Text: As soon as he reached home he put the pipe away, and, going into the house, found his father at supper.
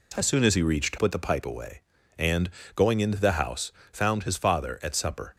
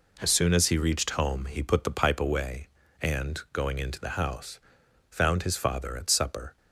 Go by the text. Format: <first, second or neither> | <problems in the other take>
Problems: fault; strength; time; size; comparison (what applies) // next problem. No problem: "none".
second | skips "home he"; at 0.9 s